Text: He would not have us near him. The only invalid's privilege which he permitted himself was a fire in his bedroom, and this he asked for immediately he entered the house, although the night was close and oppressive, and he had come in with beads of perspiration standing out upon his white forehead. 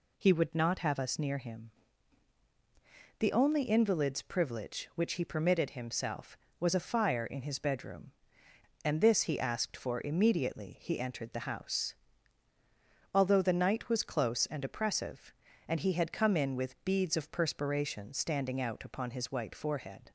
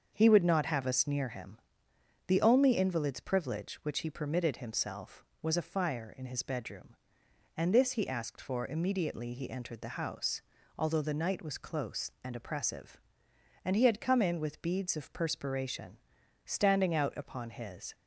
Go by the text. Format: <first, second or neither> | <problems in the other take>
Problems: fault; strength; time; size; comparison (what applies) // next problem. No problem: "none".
first | starts louder than the rest; until 1.1 s; 6.5 dB // pauses between "perspiration" and "standing"; noticeable; at 15.9 s; 0.48 s long // stops before "white forehead"; at 17.9 s